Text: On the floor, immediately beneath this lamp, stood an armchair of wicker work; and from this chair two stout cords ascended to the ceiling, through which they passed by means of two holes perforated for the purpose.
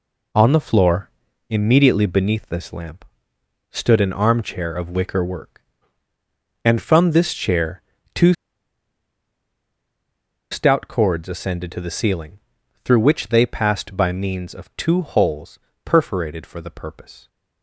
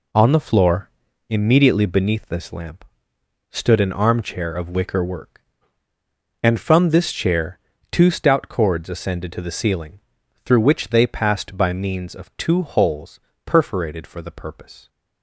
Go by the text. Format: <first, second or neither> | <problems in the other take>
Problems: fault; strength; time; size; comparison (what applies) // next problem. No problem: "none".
second | pauses between "chair" and "two"; slight; at 7.8 s; 0.32 s long; slight in the second // pauses between "two" and "stout"; strong; at 8.3 s; 2.1 s long // pauses between "holes" and "perforated"; slight; at 15.5 s; 0.24 s long; slight in the second